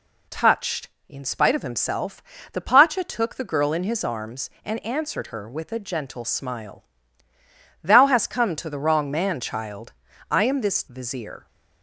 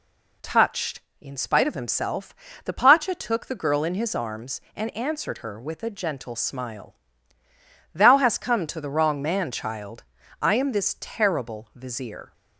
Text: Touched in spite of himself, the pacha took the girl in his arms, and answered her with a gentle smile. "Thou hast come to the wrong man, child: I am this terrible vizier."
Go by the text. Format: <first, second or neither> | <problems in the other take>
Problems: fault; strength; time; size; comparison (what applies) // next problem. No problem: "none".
second | skips "terrible"; at 10.8 s